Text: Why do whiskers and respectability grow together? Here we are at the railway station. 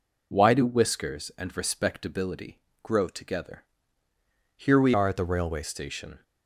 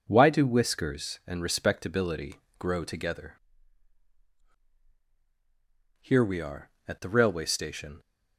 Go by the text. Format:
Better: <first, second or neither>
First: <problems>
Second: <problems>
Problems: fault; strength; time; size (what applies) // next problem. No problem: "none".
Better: second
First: pauses between "respectability" and "grow"; slight; at 2.5 s; 0.24 s long // changes voice from "are" to "railway"; from 4.9 to 5.6 s; 0.7 s long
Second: pauses between "respectability" and "grow"; slight; at 2.3 s; 0.24 s long